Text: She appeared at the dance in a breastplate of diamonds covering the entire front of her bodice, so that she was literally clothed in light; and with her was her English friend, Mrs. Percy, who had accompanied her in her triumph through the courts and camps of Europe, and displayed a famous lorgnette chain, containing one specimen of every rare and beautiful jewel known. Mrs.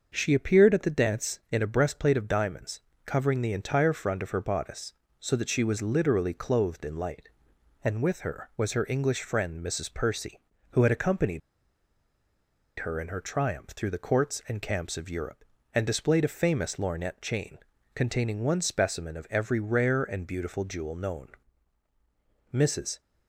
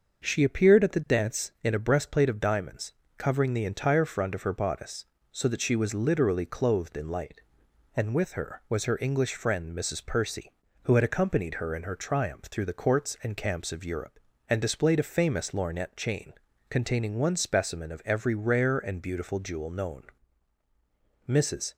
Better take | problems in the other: second | starts louder than the rest; until 1.1 s; 6.5 dB; noticeable in the second // pauses between "diamonds" and "covering"; slight; at 2.8 s; 0.26 s long; slight in the second // pauses between "accompanied" and "her"; strong; at 11.4 s; 1.4 s long

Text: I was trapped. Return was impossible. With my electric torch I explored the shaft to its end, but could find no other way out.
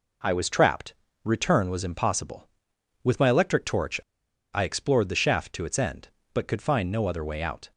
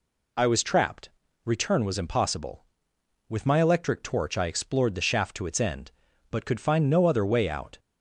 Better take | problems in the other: second | pauses between "torch" and "I"; noticeable; at 3.9 s; 0.53 s long

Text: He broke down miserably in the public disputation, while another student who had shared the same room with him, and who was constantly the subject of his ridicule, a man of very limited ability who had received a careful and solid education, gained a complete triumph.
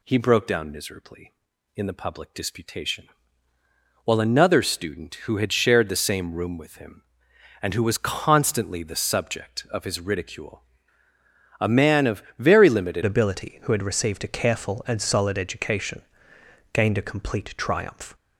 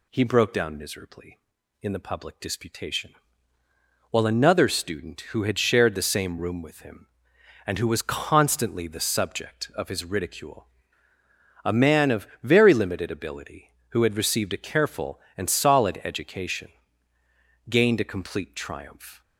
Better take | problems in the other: second | pauses between "of" and "very"; slight; at 12.2 s; 0.16 s long; slight in the second // changes voice at "ability"; from 13.0 s on; 5.1 s long

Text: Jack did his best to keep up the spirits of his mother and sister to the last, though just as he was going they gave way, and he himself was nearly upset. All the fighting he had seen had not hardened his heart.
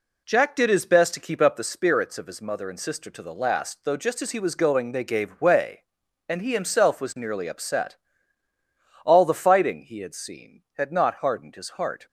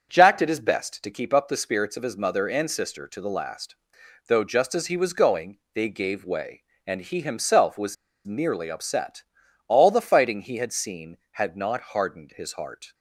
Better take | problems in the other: first | starts louder than the rest; until 1.1 s; 7 dB // pauses between "going" and "they"; slight; at 5.5 s; 0.16 s long // pauses between "was" and "nearly"; slight; at 7.9 s; 0.30 s long

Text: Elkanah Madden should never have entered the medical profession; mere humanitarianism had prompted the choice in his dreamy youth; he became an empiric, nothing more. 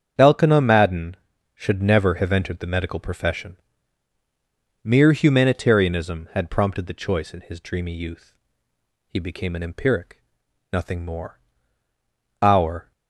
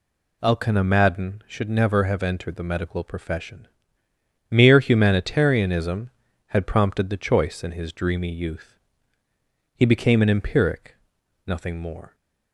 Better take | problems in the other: second | starts louder than the rest; strong; until 1.6 s; 8 dB // goes on to say "Our"; slight; from 12.4 s on; 0.48 s long

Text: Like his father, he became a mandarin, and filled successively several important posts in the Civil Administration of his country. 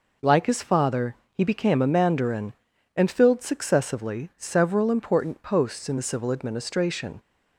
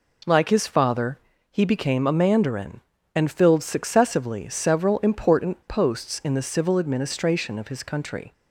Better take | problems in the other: second | stops before "of his country"; at 7.1 s

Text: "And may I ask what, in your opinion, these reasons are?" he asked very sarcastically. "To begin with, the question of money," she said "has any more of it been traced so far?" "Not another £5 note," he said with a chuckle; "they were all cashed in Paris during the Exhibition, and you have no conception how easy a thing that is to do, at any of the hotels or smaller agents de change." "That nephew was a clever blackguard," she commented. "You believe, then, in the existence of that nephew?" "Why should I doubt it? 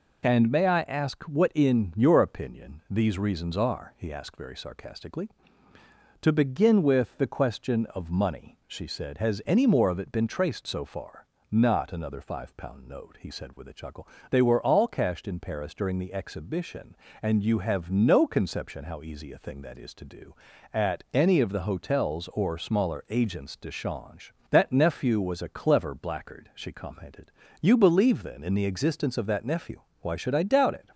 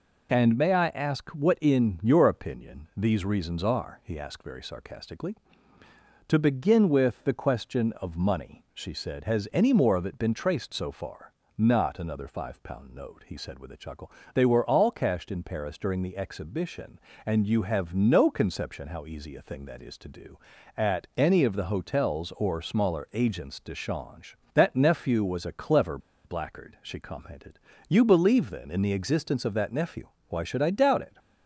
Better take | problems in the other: first | pauses between "clever" and "blackguard"; slight; at 25.9 s; 0.26 s long

